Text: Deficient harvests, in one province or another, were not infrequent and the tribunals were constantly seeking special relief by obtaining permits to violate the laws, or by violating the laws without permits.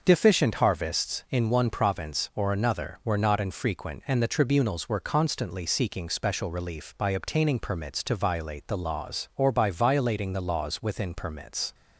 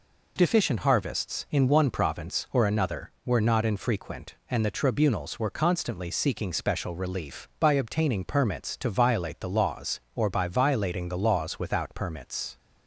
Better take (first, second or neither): second